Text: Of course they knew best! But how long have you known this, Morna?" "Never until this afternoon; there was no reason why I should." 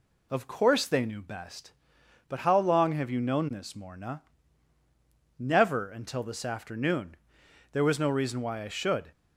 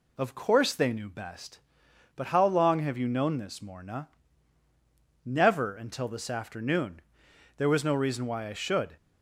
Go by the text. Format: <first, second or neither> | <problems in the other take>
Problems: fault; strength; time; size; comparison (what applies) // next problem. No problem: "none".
neither | none